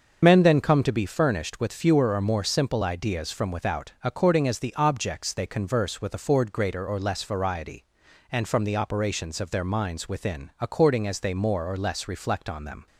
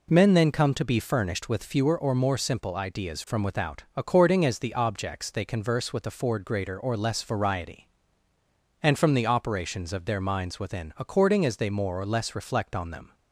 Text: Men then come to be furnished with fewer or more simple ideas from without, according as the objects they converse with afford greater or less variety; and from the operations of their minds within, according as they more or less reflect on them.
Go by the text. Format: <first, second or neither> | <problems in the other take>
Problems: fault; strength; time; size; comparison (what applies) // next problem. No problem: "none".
second | loses the start of "Men"; at 0.2 s; 80 ms // starts louder than the rest; until 1.2 s; 6.5 dB